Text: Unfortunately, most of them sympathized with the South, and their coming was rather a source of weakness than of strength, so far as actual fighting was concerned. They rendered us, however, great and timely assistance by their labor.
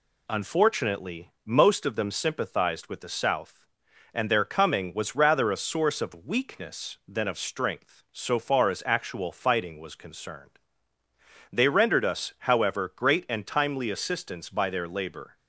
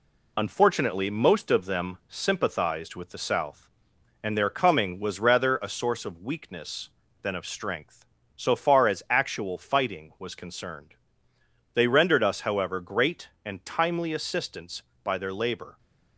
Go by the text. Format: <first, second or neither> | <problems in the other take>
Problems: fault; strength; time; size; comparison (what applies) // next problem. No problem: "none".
first | gets quieter; slight; throughout; 2.5 dB